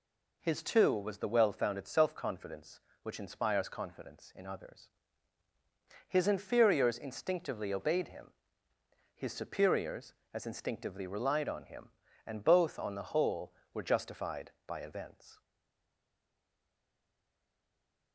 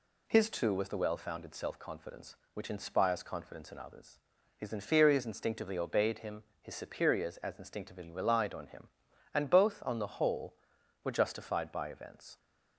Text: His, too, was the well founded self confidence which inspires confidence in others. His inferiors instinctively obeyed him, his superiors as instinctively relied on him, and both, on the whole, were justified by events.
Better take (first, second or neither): second